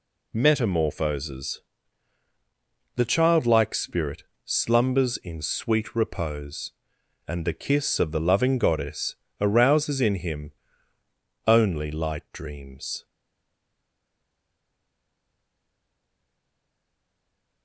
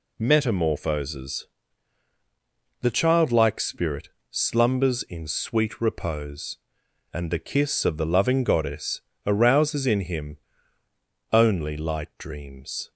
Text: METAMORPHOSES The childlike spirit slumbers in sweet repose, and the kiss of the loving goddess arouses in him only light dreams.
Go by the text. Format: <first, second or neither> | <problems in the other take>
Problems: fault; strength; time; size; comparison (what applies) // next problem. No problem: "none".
second | pauses between "METAMORPHOSES" and "The"; strong; at 1.6 s; 1.3 s long; strong in the second // pauses between "spirit" and "slumbers"; slight; at 4.2 s; 0.24 s long; slight in the second // pauses between "goddess" and "arouses"; slight; at 9.1 s; 0.26 s long; slight in the second // pauses between "him" and "only"; noticeable; at 10.5 s; 0.96 s long; noticeable in the second // stays silent after the last word; strong; from 13.0 s on; 4.6 s long